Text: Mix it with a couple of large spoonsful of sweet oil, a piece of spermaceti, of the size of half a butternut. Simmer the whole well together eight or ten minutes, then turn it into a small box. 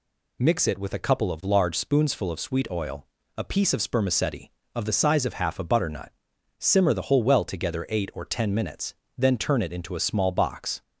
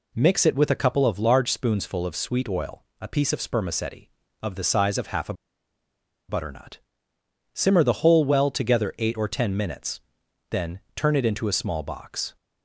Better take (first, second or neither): first